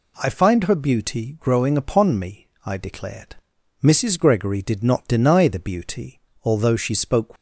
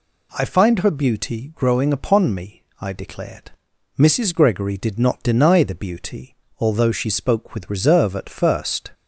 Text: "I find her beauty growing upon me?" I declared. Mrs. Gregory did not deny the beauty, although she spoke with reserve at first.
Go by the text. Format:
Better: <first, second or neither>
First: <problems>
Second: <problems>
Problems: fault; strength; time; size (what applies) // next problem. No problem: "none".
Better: second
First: stops before "with reserve at first"; at 7.3 s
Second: none